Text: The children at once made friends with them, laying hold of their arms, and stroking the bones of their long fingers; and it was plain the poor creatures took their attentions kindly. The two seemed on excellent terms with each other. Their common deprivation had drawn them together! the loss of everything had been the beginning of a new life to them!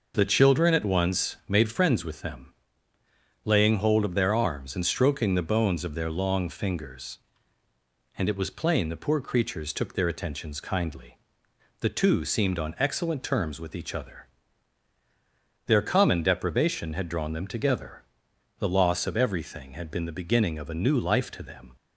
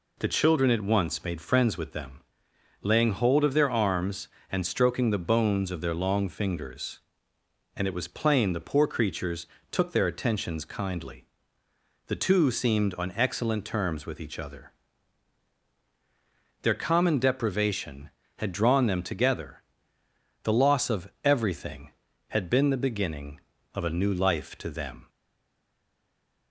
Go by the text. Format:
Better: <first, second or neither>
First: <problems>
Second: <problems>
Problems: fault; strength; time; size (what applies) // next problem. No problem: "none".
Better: first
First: none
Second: pauses between "creatures" and "took"; slight; at 9.4 s; 0.24 s long // stays silent after the last word; noticeable; from 25.0 s on; 1.5 s long